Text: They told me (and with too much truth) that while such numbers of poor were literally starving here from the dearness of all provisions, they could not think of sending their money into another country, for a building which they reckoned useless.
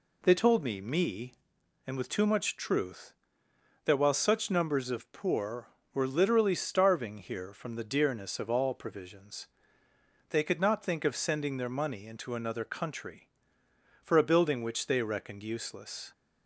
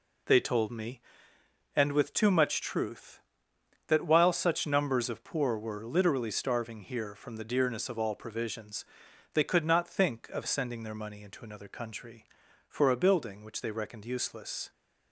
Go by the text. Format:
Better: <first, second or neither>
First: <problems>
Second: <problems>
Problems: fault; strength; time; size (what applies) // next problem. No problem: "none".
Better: second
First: says "me" twice; at 0.7 s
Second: none